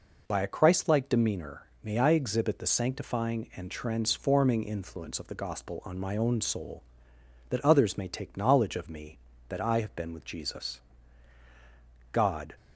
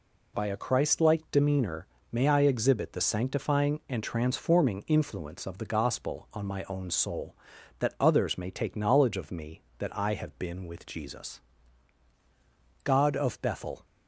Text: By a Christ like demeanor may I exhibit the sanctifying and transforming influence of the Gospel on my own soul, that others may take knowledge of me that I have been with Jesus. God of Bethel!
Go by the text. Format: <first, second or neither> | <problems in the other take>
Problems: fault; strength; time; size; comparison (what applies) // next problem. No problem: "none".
second | pauses between "demeanor" and "may"; slight; at 1.6 s; 0.16 s long; slight in the second // stops before "of Bethel"; at 12.5 s